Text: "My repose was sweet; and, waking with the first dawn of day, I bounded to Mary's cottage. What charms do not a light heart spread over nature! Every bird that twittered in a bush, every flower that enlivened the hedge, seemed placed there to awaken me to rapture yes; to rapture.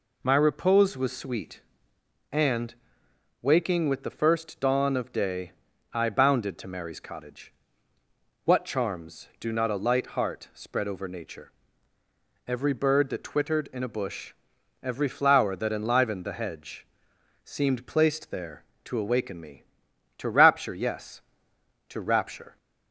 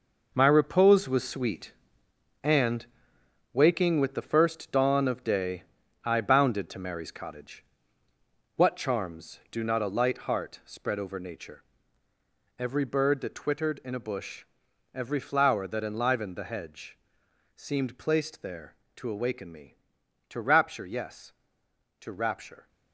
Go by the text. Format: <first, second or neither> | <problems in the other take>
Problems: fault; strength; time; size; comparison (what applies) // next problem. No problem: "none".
first | gets quieter; strong; throughout; 9.5 dB